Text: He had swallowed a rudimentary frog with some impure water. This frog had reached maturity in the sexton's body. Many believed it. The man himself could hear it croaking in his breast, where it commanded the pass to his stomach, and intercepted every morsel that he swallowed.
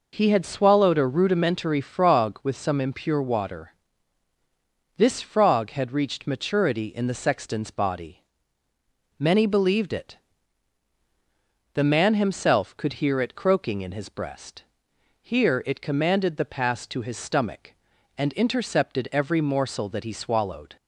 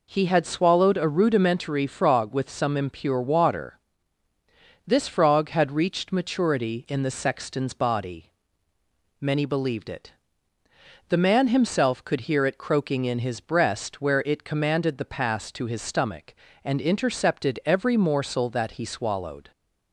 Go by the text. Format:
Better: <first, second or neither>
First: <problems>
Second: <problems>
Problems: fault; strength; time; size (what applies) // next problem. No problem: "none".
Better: second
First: says "here" for "where"; at 15.1 s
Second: none